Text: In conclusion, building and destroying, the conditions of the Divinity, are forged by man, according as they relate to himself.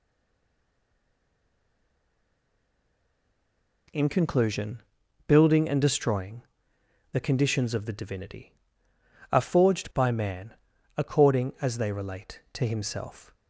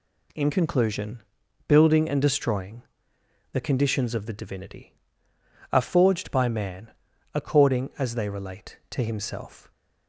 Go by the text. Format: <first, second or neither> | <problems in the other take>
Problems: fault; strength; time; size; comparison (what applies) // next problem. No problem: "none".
second | stays silent before the first word; strong; until 3.8 s; 3.8 s long